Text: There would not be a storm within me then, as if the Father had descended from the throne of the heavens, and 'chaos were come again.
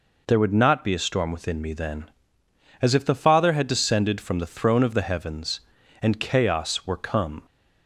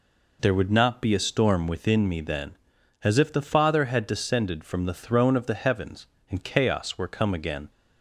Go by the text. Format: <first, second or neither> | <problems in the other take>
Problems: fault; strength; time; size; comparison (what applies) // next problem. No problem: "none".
second | stops before "again"; at 7.4 s